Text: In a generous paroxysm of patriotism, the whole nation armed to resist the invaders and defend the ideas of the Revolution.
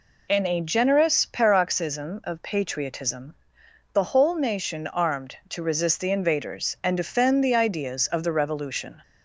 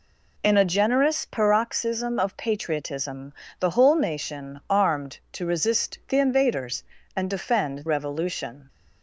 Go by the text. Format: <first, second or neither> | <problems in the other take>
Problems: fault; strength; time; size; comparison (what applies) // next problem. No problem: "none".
first | skips "the ideas of the"; at 7.8 s